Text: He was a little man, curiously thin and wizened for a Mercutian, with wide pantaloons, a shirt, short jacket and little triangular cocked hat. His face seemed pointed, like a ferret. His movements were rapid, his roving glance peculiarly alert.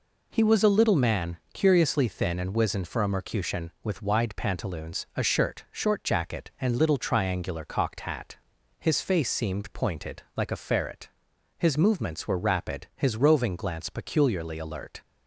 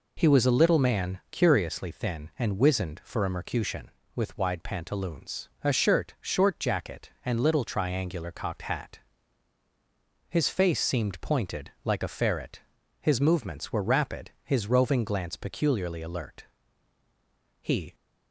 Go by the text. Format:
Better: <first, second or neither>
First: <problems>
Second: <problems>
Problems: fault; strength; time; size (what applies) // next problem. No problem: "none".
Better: first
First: none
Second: goes on to say "He"; slight; from 17.6 s on; 0.34 s long